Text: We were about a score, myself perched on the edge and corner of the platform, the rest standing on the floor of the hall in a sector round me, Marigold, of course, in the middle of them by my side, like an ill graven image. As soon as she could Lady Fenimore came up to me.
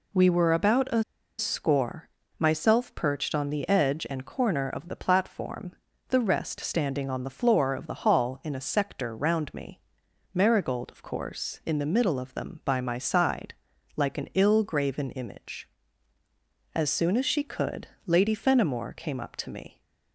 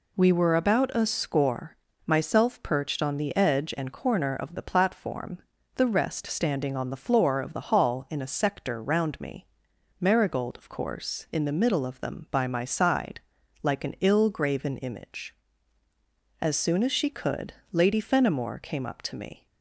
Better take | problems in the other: second | pauses between "a" and "score"; slight; at 1.0 s; 0.35 s long // pauses between "could" and "Lady"; slight; at 17.8 s; 0.16 s long; slight in the second

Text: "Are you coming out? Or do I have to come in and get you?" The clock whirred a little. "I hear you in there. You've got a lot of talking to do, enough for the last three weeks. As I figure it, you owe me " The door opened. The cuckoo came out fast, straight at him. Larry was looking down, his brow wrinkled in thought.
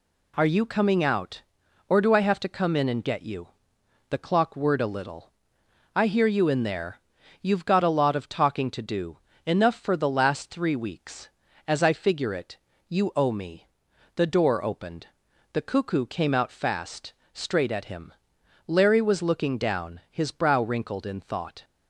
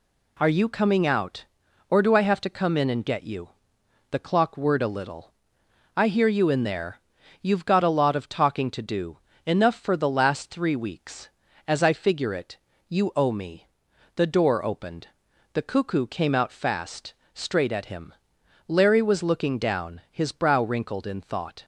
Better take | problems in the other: neither | none

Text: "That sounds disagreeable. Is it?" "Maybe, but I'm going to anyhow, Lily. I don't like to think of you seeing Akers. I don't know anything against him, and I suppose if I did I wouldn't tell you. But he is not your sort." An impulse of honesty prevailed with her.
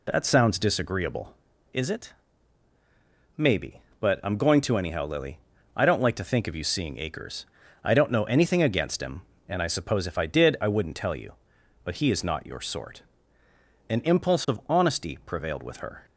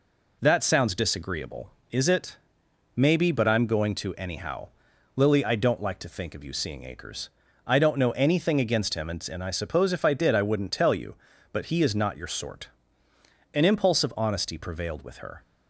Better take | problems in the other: first | says "and" twice; at 9.3 s

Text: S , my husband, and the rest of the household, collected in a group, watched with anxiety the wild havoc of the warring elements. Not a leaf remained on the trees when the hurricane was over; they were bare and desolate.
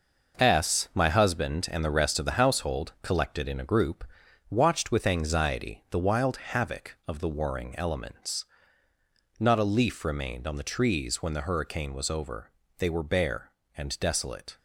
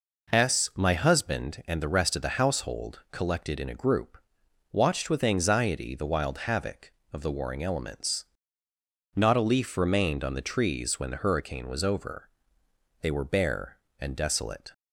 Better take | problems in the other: second | gets quieter; strong; throughout; 8 dB

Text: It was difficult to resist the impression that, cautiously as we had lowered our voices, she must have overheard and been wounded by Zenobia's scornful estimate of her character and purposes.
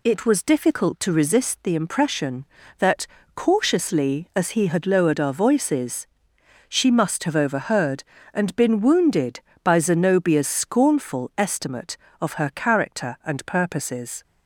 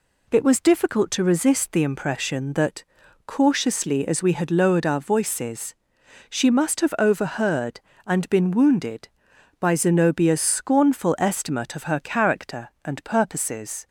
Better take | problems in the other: second | says "he" for "we"; at 4.5 s

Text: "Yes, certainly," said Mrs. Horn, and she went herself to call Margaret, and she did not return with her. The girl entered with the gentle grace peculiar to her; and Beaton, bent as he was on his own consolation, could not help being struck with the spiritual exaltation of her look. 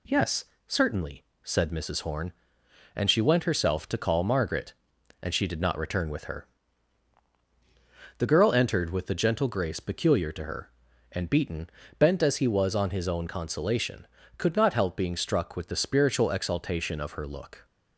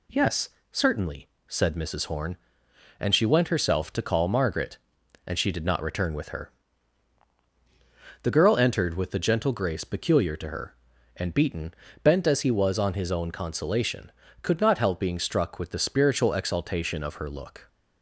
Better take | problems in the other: neither | none

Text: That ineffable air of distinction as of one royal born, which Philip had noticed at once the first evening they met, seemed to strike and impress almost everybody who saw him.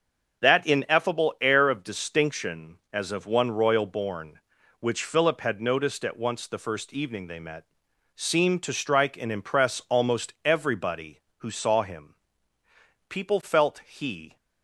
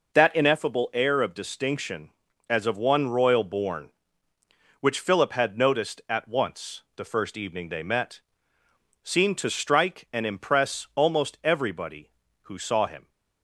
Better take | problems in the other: second | starts louder than the rest; until 1.4 s; 6.5 dB // goes on to say "People felt he"; noticeable; from 13.0 s on; 1.2 s long

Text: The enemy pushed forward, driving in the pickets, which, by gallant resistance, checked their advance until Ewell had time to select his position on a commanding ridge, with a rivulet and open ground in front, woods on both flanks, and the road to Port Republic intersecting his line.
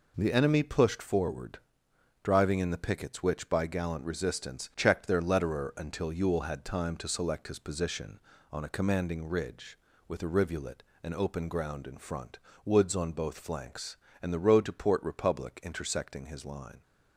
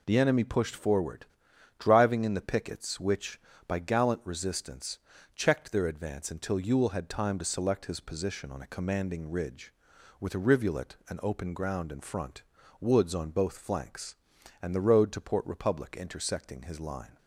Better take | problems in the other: second | says "letterer" for "advance"; at 5.1 s

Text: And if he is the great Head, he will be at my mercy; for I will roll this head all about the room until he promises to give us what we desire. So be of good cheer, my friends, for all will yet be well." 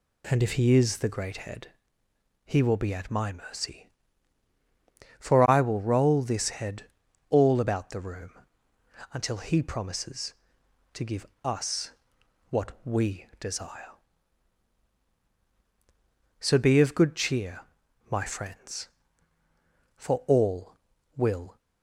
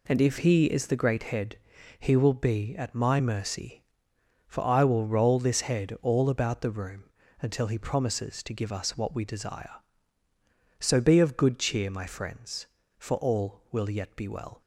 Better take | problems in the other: second | pauses between "head" and "all"; noticeable; at 6.8 s; 0.46 s long // pauses between "room" and "until"; noticeable; at 8.3 s; 0.82 s long; slight in the second // pauses between "give" and "us"; slight; at 11.2 s; 0.20 s long // pauses between "us" and "what"; noticeable; at 11.9 s; 0.58 s long // stops before "yet be well"; at 21.5 s

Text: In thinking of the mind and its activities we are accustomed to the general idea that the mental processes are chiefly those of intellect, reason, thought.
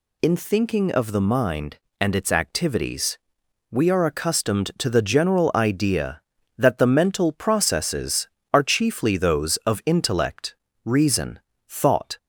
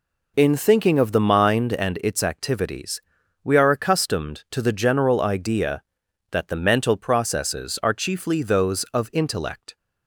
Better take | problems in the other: first | pauses between "activities" and "we"; at 2.9 s; 0.44 s long; noticeable in the first // stops before "reason thought"; at 9.7 s

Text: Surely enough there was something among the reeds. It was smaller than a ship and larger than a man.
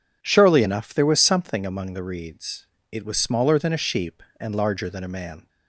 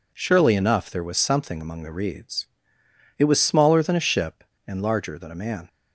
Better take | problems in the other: second | says "sheep" for "ship"; at 3.7 s

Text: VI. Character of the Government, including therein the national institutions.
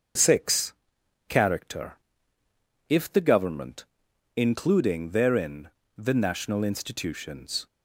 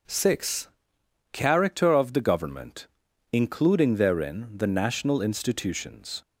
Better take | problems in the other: second | starts louder than the rest; until 1.7 s; 6.5 dB // says "if" for "of"; at 2.8 s // pauses between "therein" and "the"; slight; at 5.6 s; 0.30 s long

